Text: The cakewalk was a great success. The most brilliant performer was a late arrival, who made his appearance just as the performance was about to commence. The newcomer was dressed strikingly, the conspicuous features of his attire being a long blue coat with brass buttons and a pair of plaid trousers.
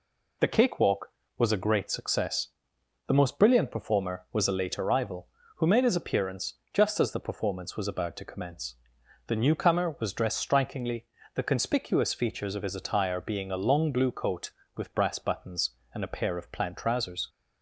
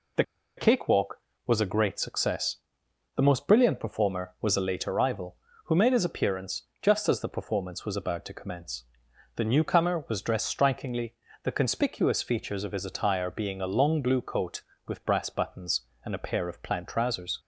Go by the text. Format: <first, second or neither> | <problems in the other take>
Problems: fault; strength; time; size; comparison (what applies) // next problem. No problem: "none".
first | pauses between "The" and "cakewalk"; slight; at 0.2 s; 0.34 s long // pauses between "appearance" and "just"; slight; at 6.6 s; 0.18 s long; slight in the first